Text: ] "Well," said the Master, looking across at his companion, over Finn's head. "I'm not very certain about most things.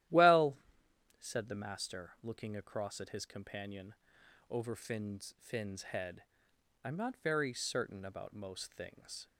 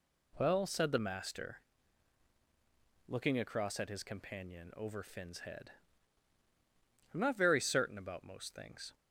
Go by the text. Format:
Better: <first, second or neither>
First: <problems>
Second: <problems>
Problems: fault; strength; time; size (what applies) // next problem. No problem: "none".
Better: second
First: starts louder than the rest; strong; until 1.7 s; 13 dB // says "Finn's" twice; at 5.4 s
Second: none